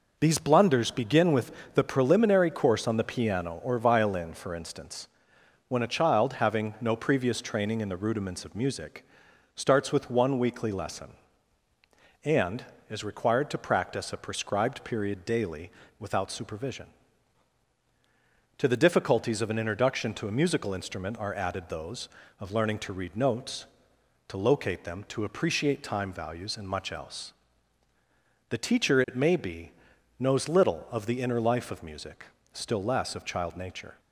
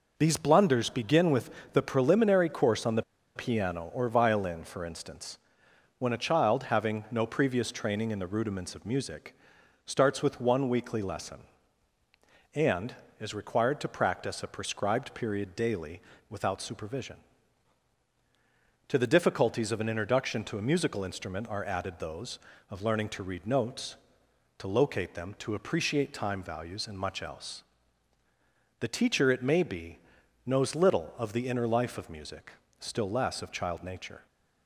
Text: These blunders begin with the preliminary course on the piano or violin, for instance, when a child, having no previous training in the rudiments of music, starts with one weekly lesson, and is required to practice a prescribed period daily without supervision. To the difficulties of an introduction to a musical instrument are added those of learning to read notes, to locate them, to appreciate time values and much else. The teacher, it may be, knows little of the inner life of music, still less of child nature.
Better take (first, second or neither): first